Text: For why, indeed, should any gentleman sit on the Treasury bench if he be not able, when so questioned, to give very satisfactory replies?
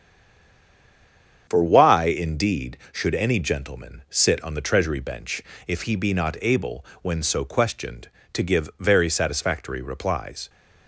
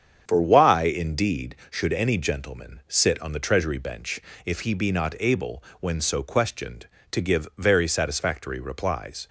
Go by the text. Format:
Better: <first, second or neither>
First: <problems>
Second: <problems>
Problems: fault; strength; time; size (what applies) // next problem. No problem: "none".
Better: second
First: stays silent before the first word; noticeable; until 1.4 s; 1.4 s long // starts louder than the rest; strong; until 2.5 s; 7.5 dB // pauses between "bench" and "if"; slight; at 5.4 s; 0.24 s long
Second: starts louder than the rest; strong; until 1.2 s; 7.5 dB // pauses between "bench" and "if"; slight; at 4.1 s; 0.24 s long